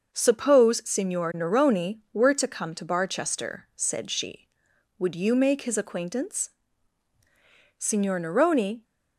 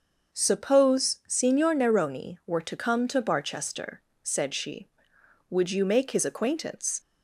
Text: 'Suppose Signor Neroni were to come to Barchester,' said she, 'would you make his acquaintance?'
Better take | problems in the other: second | starts louder than the rest; until 1.2 s; 6 dB; also in the second // goes on to say "Signor Neroni"; noticeable; from 7.7 s on; 1.0 s long

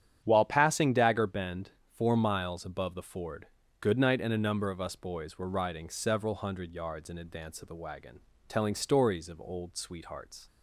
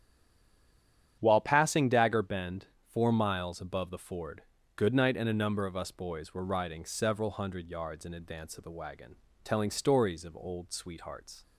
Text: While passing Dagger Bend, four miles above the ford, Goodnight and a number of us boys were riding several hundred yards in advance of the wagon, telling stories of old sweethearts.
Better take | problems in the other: first | stays silent before the first word; noticeable; until 1.2 s; 1.2 s long // starts louder than the rest; strong; until 2.2 s; 9 dB; strong in the first

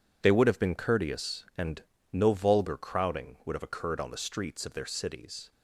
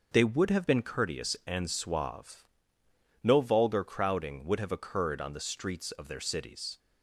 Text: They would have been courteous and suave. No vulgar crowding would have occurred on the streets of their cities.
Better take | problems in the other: second | skips "suave"; at 1.9 s

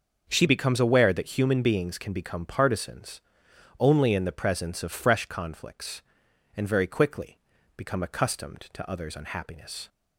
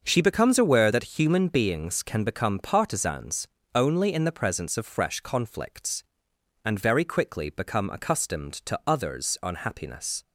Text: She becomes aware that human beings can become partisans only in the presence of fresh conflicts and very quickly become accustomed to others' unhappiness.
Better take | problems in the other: second | starts louder than the rest; until 1.3 s; 6.5 dB; also in the second // changes voice at "becomes"; from 0.4 s on; 9.4 s long // pauses between "partisans" and "only"; noticeable; at 3.2 s; 0.60 s long; slight in the second // pauses between "quickly" and "become"; at 7.3 s; 0.38 s long

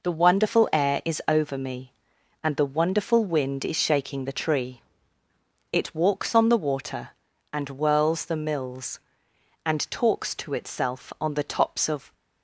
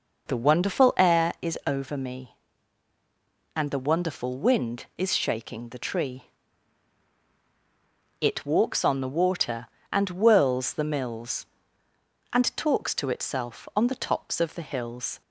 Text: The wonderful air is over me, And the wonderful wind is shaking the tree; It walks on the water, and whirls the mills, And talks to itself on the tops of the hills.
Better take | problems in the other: second | stops before "the hills"; at 12.1 s

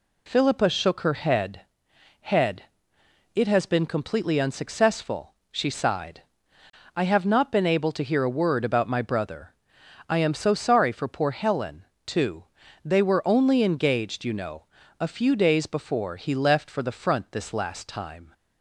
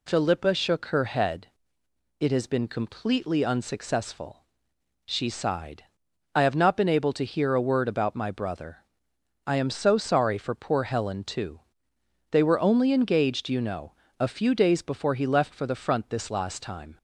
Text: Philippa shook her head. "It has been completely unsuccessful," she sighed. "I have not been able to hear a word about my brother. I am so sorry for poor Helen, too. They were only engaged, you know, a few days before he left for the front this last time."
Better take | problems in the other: second | says "head" twice; at 2.1 s

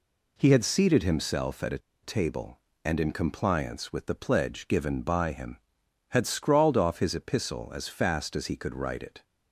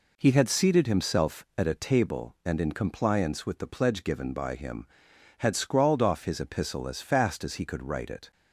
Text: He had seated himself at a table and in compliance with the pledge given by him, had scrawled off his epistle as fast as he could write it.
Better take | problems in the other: second | pauses between "a" and "table"; slight; at 1.7 s; 0.23 s long

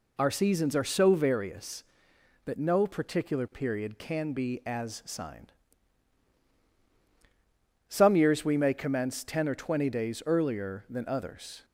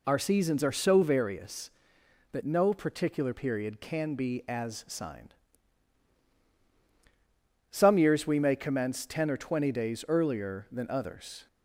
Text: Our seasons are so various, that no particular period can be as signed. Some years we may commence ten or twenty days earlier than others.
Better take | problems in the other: neither | none

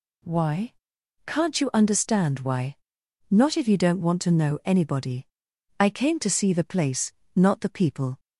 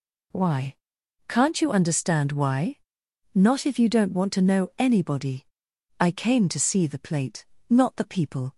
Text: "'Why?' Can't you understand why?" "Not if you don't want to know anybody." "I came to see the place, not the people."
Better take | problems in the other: first | says "plate" for "place"; at 6.9 s

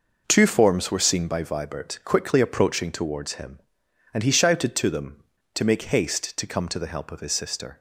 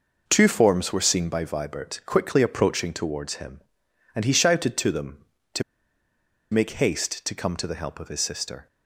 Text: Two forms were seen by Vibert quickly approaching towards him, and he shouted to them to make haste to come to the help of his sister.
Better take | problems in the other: first | pauses between "to" and "make"; noticeable; at 5.6 s; 0.89 s long

